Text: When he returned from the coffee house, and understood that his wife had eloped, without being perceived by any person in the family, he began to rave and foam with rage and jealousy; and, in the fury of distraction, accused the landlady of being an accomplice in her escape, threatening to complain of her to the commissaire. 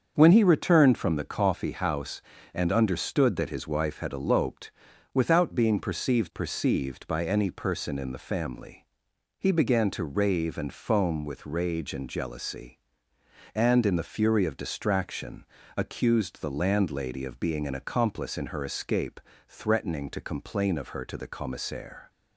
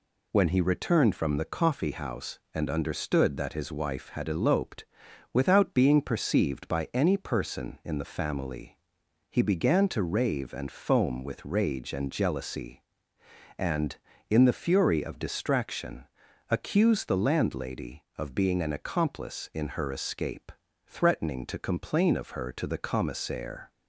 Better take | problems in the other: second | starts louder than the rest; until 1.1 s; 7 dB // says "perceived" twice; at 6.3 s

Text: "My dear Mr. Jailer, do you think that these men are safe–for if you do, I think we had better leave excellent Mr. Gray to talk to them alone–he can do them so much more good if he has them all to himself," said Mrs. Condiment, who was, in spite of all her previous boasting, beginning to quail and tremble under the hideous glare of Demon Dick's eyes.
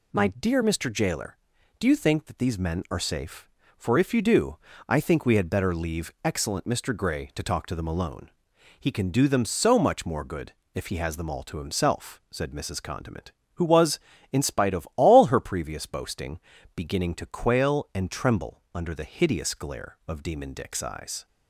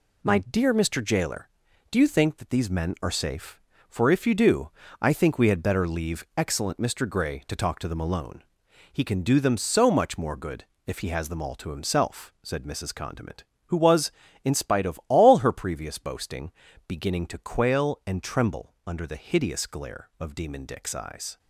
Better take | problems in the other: first | gets quieter; throughout; 6.5 dB // pauses between "good" and "if"; slight; at 10.6 s; 0.20 s long; slight in the first

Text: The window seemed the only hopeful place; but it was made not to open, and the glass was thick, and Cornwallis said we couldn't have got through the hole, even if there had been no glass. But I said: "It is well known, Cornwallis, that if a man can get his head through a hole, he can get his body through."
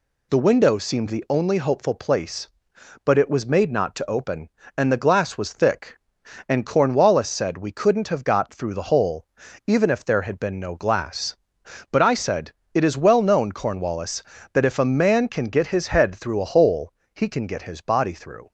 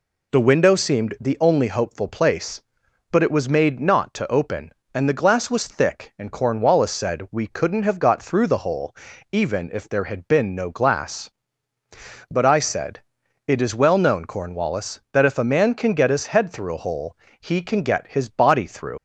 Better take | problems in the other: first | leaves "through" unfinished; at 18.9 s; 90 ms

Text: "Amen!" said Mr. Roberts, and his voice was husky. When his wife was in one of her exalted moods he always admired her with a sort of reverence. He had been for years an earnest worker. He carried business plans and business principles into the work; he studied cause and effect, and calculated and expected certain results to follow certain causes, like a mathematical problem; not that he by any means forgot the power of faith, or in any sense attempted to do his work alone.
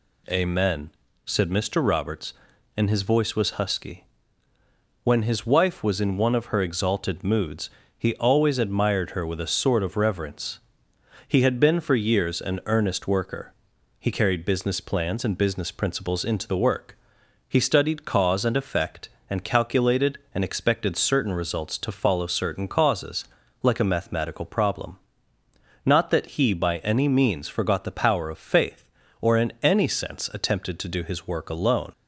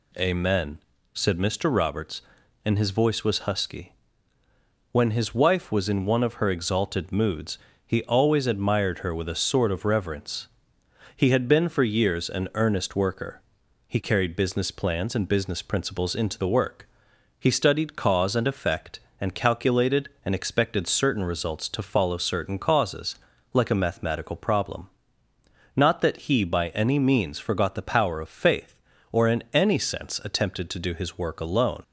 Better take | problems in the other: neither | pauses between "moods" and "he"; slight; the same in both

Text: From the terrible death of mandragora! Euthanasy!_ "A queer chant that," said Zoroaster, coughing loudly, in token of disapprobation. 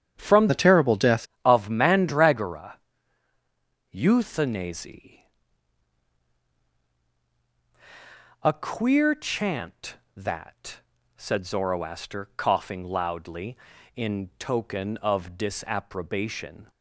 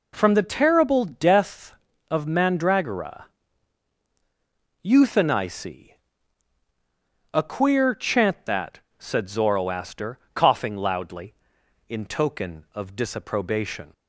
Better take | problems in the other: second | starts louder than the rest; strong; until 1.1 s; 8.5 dB // changes voice from "the" to "death"; from 0.4 to 1.2 s; 0.8 s long

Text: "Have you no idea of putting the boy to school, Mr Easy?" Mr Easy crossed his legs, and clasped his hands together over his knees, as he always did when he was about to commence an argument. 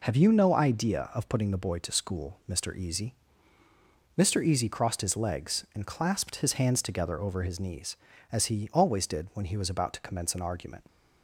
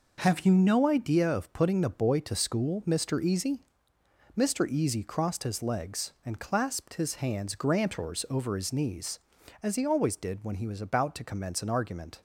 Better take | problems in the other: first | says "grantors" for "together"; at 7.5 s

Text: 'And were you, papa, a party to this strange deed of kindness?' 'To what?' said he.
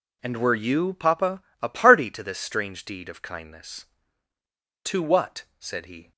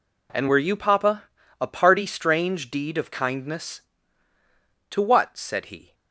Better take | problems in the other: first | skips "to this"; at 2.0 s

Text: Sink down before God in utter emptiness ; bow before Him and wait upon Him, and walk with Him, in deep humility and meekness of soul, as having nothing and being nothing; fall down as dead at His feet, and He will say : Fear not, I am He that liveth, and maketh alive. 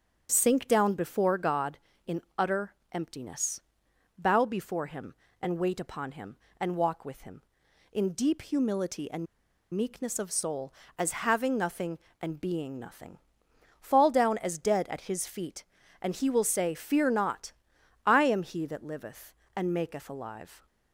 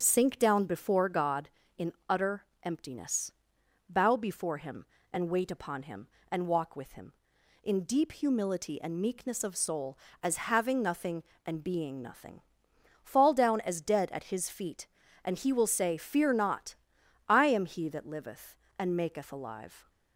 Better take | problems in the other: second | starts louder than the rest; strong; until 1.3 s; 7.5 dB; strong in the second // pauses between "in" and "utter"; slight; at 2.2 s; 0.16 s long; slight in the second // pauses between "utter" and "emptiness"; slight; at 2.7 s; 0.18 s long; slight in the second // pauses between "and" and "meekness"; noticeable; at 9.2 s; 0.48 s long

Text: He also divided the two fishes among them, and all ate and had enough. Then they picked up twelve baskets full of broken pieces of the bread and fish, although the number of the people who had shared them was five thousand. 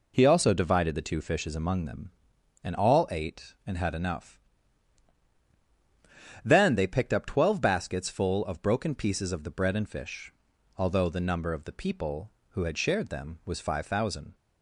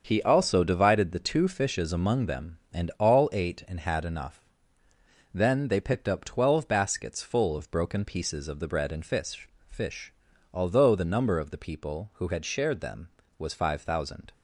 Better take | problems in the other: first | starts louder than the rest; until 1.0 s; 7 dB // says "fish" twice; at 9.6 s

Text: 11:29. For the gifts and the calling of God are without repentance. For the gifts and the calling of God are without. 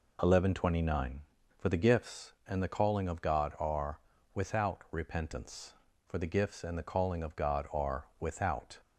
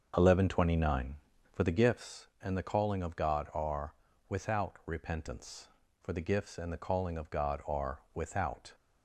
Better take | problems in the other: first | starts louder than the rest; until 1.8 s; 6.5 dB // pauses between "are" and "without"; slight; at 3.9 s; 0.34 s long; slight in the first // pauses between "are" and "without"; slight; at 7.9 s; 0.16 s long; slight in the first

